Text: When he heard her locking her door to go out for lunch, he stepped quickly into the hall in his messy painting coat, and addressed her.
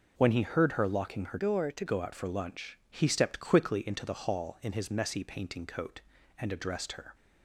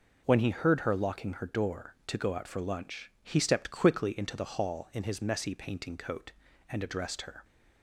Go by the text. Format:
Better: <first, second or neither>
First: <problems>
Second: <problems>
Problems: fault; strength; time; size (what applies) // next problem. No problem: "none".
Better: second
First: changes voice from "door" to "to"; from 1.3 to 1.8 s; 0.5 s long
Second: none